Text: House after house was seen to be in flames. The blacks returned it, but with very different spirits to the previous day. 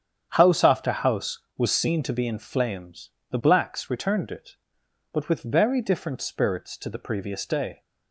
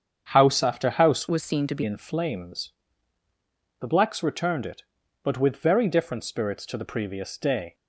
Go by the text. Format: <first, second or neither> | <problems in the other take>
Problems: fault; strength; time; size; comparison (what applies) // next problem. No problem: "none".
first | starts louder than the rest; strong; until 1.3 s; 7.5 dB; strong in the first // changes voice from "was" to "be"; from 1.2 to 1.8 s; 0.6 s long